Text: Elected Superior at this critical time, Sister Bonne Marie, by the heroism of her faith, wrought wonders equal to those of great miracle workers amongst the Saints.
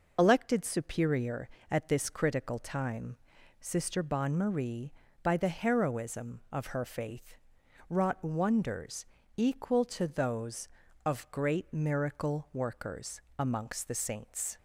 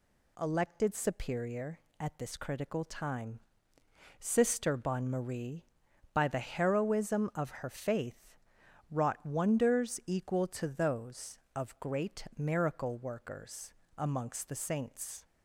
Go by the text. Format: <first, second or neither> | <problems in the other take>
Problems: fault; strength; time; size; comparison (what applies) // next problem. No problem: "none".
second | loses the start of "Elected"; at 0.1 s; 50 ms // pauses between "wonders" and "equal"; slight; at 9.0 s; 0.32 s long // pauses between "workers" and "amongst"; slight; at 13.2 s; 0.18 s long; slight in the second